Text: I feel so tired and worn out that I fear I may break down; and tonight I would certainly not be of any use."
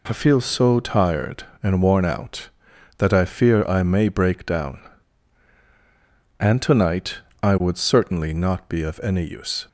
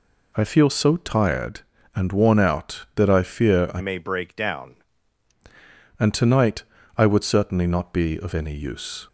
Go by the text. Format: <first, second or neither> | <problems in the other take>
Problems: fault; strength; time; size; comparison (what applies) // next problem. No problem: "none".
first | changes voice from "may" to "down"; from 3.7 to 4.7 s; 1.0 s long // pauses between "tonight" and "I"; slight; at 6.6 s; 0.34 s long; slight in the first